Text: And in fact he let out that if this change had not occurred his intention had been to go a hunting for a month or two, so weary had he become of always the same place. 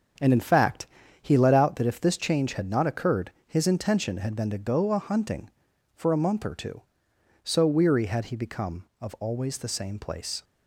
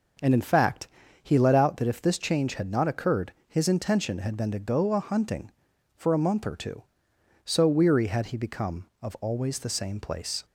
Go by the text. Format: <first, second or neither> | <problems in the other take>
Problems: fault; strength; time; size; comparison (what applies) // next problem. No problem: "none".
second | gets quieter; strong; throughout; 7.5 dB // pauses between "fact" and "he"; slight; at 0.8 s; 0.36 s long; slight in the second